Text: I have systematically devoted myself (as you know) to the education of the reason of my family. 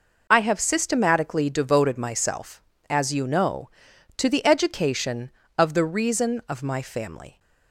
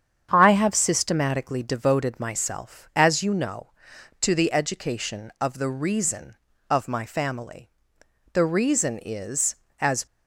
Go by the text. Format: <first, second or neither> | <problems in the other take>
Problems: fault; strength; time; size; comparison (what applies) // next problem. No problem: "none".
first | starts louder than the rest; strong; until 1.3 s; 8 dB // goes on to say "The reason is as"; strong; from 8.3 s on; 1.7 s long